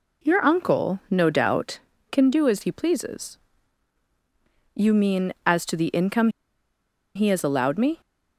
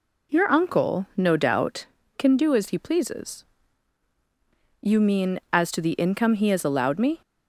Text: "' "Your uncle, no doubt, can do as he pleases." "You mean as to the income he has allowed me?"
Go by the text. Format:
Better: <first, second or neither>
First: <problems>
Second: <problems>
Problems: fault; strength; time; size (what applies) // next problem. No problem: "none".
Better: second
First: pauses between "income" and "he"; noticeable; at 6.2 s; 0.87 s long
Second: none